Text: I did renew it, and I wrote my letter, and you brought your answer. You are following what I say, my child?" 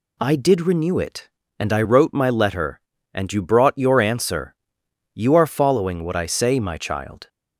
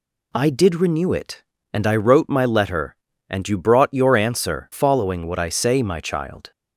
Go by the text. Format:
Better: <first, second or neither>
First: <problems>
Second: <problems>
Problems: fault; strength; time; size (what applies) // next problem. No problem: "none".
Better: first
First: none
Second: skips "You are"; at 4.7 s